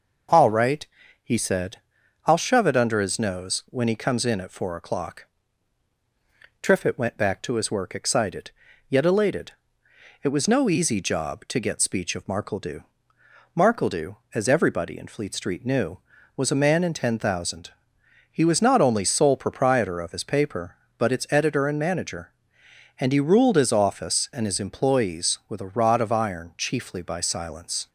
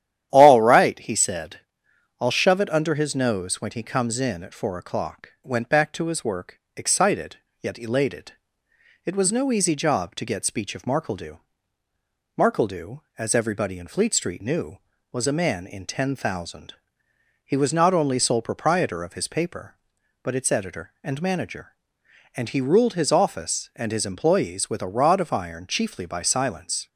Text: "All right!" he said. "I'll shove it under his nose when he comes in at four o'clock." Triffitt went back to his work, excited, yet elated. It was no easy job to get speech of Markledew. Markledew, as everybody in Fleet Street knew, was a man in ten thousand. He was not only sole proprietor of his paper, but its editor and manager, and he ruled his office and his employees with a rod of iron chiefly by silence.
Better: first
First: none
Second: starts louder than the rest; strong; until 1.3 s; 11 dB // skips "Triffitt"; at 5.3 s

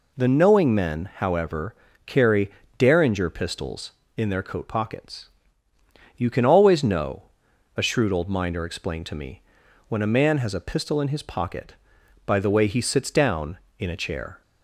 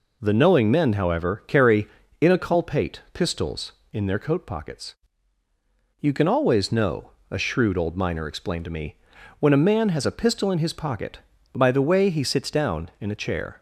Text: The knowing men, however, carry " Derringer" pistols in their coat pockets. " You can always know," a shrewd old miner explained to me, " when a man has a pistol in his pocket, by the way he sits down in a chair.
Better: first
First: none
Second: says "Inculpate" for "Derringer"; at 2.2 s

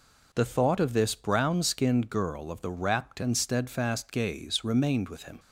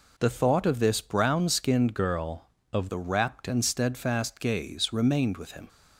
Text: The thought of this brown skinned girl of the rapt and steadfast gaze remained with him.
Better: first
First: none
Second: changes voice from "girl" to "of"; from 1.9 to 2.8 s; 0.9 s long

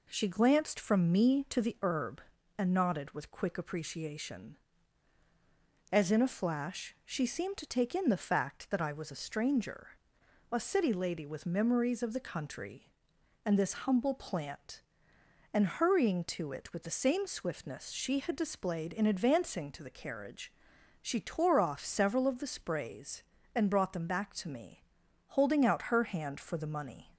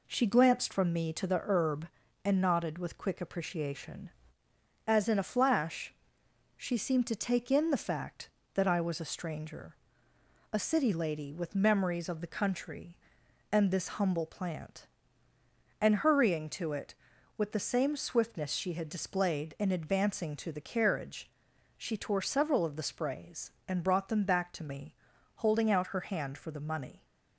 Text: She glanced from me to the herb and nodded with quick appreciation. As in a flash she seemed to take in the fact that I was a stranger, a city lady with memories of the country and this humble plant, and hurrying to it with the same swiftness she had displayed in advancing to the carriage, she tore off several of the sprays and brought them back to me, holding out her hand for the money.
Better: first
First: none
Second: pauses between "flash" and "she"; noticeable; at 5.9 s; 0.62 s long // skips "off"; at 22.2 s

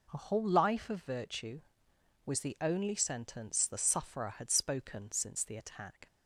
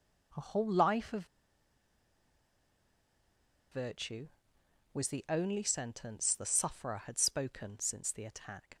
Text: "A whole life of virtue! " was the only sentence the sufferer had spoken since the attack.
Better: first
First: none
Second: pauses between "of" and "virtue"; strong; at 1.2 s; 2.4 s long

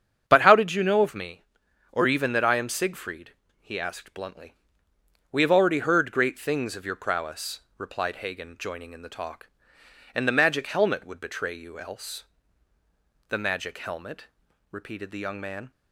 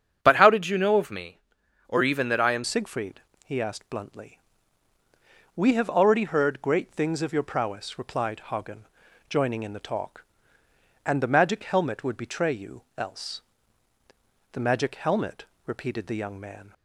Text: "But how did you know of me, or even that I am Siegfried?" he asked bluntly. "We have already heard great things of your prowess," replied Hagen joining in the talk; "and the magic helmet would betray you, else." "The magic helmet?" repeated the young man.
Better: first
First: starts louder than the rest; strong; until 1.3 s; 8 dB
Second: starts louder than the rest; strong; until 1.2 s; 8 dB // changes voice at "Siegfried"; from 2.6 s on; 14.1 s long // pauses between "Hagen" and "joining"; at 8.8 s; 0.42 s long

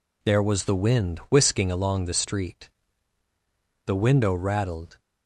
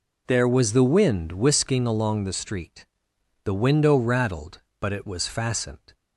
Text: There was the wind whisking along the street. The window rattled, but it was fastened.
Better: second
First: stops before "but it was fastened"; at 4.9 s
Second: none

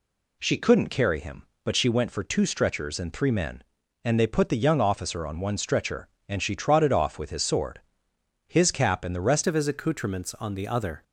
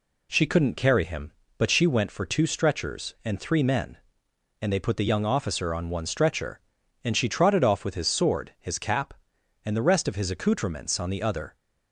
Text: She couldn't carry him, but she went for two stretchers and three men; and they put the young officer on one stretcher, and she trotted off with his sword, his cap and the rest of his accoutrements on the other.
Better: second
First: changes voice at "of"; from 9.4 s on; 1.6 s long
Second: none

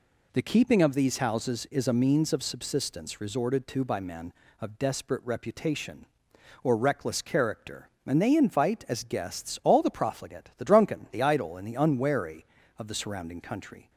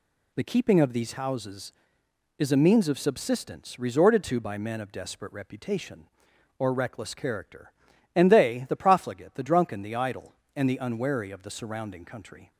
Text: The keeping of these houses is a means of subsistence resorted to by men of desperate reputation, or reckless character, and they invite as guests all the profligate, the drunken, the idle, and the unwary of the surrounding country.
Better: first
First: none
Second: skips "invite as guests all"; at 8.6 s

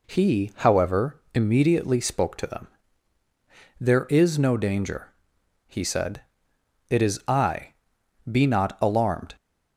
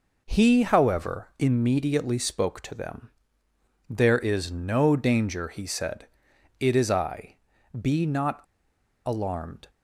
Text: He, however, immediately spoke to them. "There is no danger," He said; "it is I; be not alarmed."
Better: first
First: none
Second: pauses between "not" and "alarmed"; noticeable; at 8.4 s; 0.64 s long

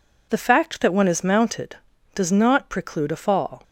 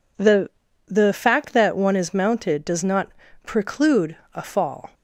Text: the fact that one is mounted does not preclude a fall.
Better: first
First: none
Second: says "the" twice; at 0.8 s // pauses between "not" and "preclude"; slight; at 3.0 s; 0.34 s long // pauses between "preclude" and "a"; slight; at 4.1 s; 0.18 s long

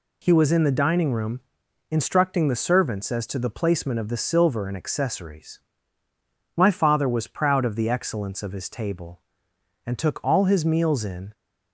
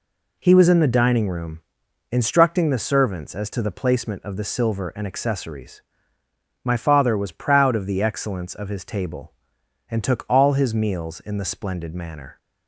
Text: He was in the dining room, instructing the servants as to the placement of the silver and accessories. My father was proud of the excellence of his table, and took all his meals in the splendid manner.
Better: second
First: stops before "the splendid manner"; at 11.3 s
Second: none

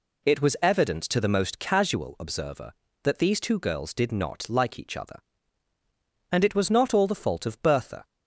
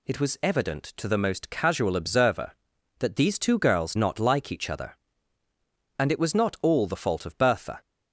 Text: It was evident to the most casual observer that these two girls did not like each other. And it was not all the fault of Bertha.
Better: first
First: none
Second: skips "did"; at 3.9 s

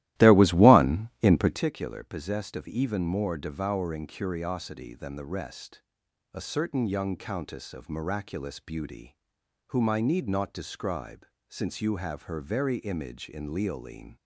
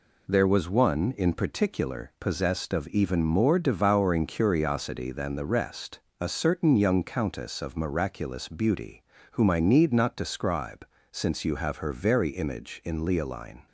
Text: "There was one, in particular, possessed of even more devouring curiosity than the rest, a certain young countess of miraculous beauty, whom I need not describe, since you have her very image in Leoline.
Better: second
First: starts louder than the rest; strong; until 1.7 s; 15.5 dB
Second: none

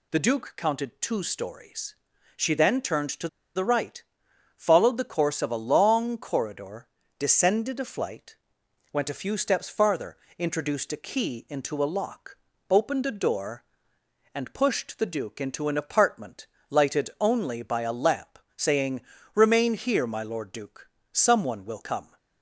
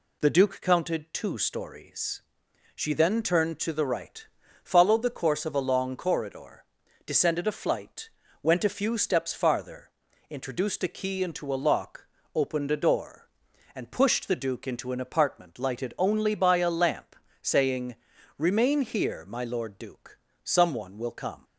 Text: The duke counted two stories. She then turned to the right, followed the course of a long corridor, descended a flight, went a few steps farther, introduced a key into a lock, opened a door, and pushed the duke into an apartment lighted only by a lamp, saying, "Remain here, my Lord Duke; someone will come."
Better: second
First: pauses between "to" and "the"; slight; at 3.2 s; 0.26 s long // pauses between "apartment" and "lighted"; slight; at 16.4 s; 0.24 s long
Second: none

